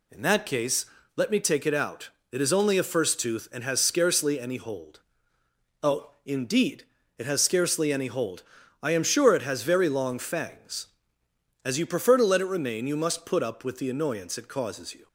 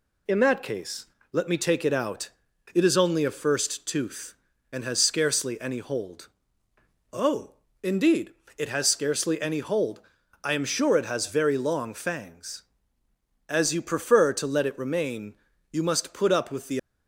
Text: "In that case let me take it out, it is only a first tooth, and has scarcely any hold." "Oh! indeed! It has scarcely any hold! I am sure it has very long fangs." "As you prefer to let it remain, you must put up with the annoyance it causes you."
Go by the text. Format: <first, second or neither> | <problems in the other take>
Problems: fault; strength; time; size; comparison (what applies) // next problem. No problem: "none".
first | pauses between "case" and "let"; slight; at 1.0 s; 0.26 s long; slight in the first // stops before "annoyance it causes you"; at 16.7 s